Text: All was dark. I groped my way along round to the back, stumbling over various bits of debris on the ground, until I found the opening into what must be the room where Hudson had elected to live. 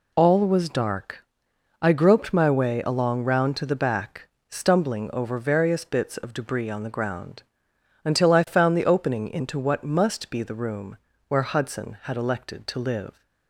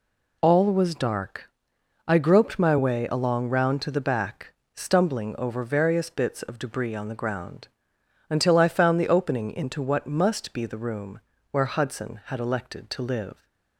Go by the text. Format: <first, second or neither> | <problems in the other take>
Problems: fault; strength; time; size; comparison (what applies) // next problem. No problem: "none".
neither | pauses between "room" and "where"; slight; the same in both